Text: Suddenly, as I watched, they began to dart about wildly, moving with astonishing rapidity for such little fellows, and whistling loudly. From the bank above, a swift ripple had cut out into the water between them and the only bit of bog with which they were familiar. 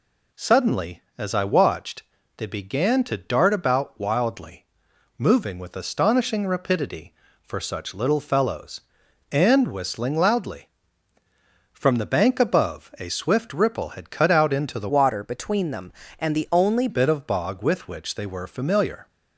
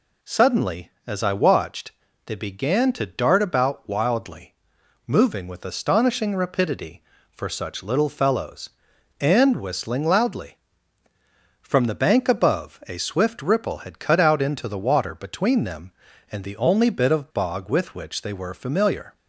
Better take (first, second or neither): second